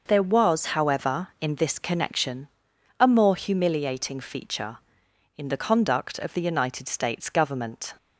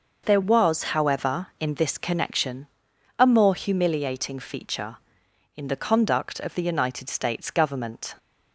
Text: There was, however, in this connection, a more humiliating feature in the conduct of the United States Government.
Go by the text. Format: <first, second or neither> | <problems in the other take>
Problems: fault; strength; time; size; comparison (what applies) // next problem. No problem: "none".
neither | none